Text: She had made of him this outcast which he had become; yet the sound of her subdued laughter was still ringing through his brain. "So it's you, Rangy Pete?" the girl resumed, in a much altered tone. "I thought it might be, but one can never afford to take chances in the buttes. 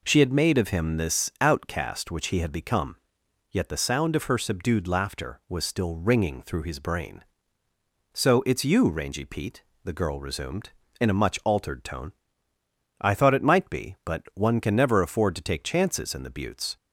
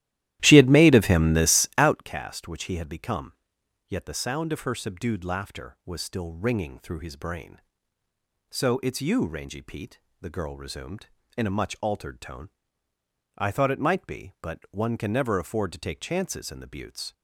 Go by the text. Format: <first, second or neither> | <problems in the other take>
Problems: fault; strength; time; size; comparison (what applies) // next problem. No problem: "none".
first | starts louder than the rest; strong; until 2.1 s; 14 dB